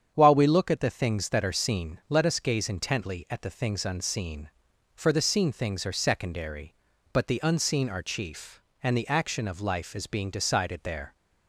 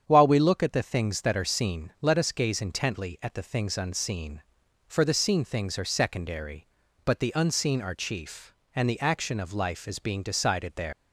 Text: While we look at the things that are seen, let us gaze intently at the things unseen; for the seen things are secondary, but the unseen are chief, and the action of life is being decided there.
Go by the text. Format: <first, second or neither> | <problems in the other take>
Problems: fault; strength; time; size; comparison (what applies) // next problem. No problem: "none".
first | starts louder than the rest; strong; until 1.0 s; 8 dB; strong in the first // leaves "there" unfinished; at 10.9 s; 150 ms